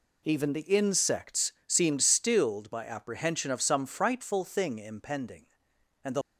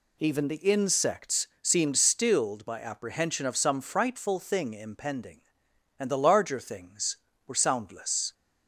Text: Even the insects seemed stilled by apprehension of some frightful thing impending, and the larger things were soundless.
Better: second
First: pauses between "insects" and "seemed"; slight; at 1.5 s; 0.16 s long // stops before "larger things were soundless"; at 6.2 s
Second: pauses between "insects" and "seemed"; slight; at 1.4 s; 0.16 s long

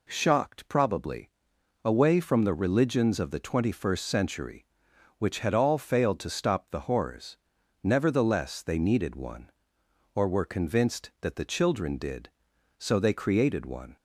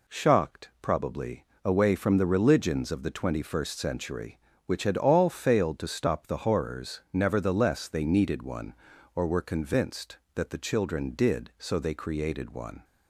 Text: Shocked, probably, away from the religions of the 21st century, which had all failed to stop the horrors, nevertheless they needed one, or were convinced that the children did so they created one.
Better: neither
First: none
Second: none

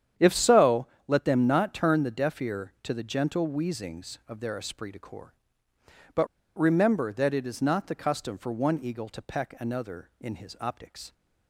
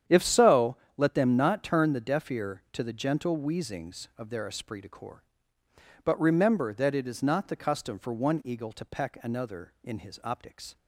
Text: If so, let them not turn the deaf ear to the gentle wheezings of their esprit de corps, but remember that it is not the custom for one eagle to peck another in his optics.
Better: second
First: starts louder than the rest; strong; until 1.3 s; 9 dB // pauses between "but" and "remember"; slight; at 6.2 s; 0.31 s long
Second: starts louder than the rest; strong; until 1.2 s; 9 dB

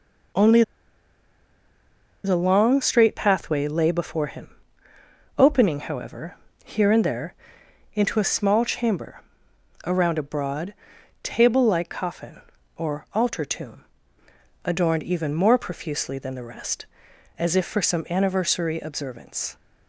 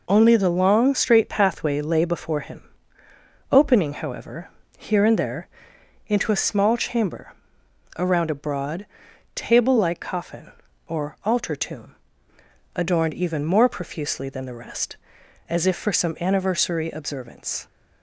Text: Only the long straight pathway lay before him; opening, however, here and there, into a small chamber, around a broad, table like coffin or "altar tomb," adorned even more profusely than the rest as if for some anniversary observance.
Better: second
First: pauses between "Only" and "the"; strong; at 0.6 s; 1.6 s long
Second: none

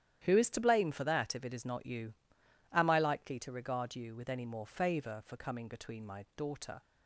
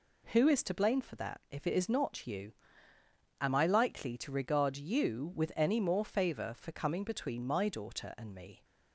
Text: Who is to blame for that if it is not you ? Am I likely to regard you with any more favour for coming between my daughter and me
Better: second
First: starts louder than the rest; strong; until 1.2 s; 11 dB // stops before "and me"; at 6.8 s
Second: none

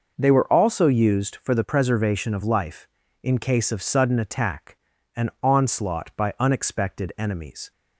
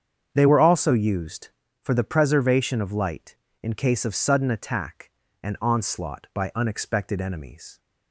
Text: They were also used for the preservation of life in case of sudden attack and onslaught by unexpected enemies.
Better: first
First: none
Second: starts louder than the rest; strong; until 1.3 s; 7.5 dB // says "light" for "life"; at 2.9 s

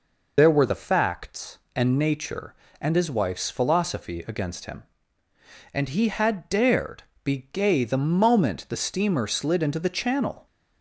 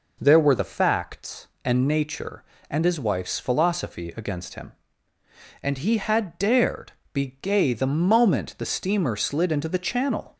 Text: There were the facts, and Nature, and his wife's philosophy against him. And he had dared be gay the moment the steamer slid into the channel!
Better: second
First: loses the start of "There"; at 0.3 s; 90 ms // pauses between "dared" and "be"; slight; at 7.0 s; 0.22 s long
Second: pauses between "dared" and "be"; slight; at 6.9 s; 0.22 s long

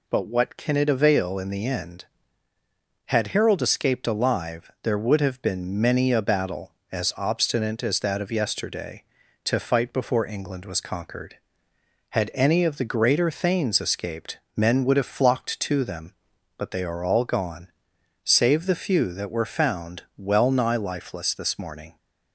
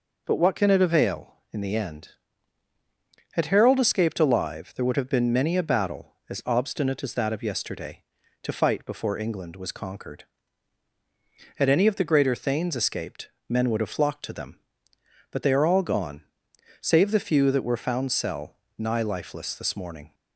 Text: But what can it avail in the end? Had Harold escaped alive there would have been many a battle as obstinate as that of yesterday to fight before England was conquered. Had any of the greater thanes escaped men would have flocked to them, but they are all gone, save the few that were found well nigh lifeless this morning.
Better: first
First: pauses between "escaped" and "men"; slight; at 14.3 s; 0.16 s long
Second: pauses between "escaped" and "men"; slight; at 13.2 s; 0.20 s long // says "cell" for "well"; at 18.0 s

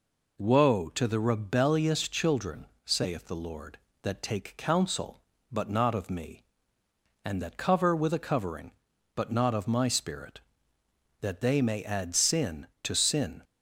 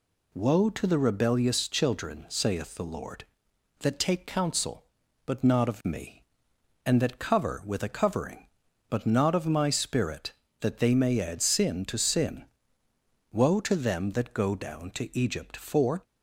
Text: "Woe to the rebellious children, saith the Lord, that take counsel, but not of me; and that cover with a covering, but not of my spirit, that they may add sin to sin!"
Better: first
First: none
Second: goes on to say "Woe to them that go down to Egypt for"; strong; from 13.3 s on; 2.7 s long

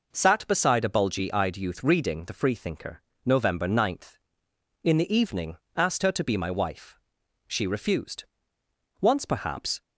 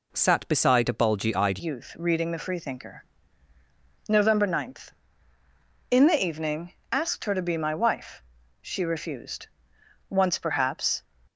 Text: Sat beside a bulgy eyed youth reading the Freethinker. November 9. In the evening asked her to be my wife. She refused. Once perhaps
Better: first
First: pauses between "evening" and "asked"; slight; at 5.5 s; 0.20 s long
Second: changes voice at "youth"; from 1.6 s on; 9.4 s long // pauses between "evening" and "asked"; slight; at 6.7 s; 0.18 s long

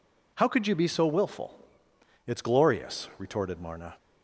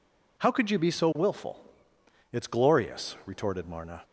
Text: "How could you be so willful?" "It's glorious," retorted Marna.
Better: neither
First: none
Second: none

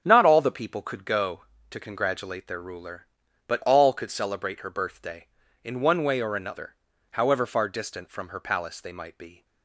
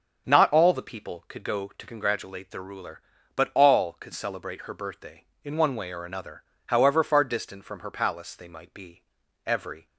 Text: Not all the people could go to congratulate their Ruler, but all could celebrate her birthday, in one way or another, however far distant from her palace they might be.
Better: first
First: starts louder than the rest; strong; until 1.0 s; 7.5 dB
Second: starts louder than the rest; until 1.3 s; 6.5 dB // goes on to say "Every"; slight; from 9.4 s on; 0.42 s long

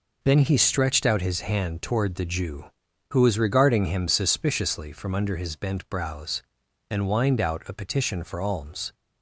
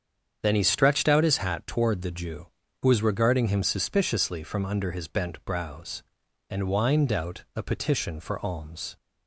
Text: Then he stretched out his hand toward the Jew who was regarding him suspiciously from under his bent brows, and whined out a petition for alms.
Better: first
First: none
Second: starts louder than the rest; strong; until 1.4 s; 8 dB // says "hat" for "hand"; at 1.3 s

